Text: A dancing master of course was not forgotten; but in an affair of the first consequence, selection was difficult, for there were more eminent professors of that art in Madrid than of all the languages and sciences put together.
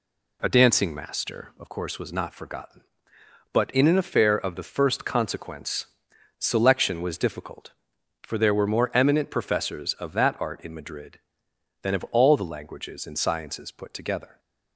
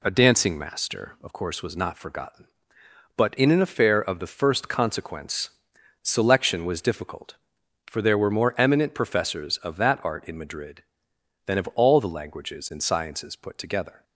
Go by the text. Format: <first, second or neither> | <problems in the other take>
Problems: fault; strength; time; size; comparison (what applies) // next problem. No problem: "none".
neither | none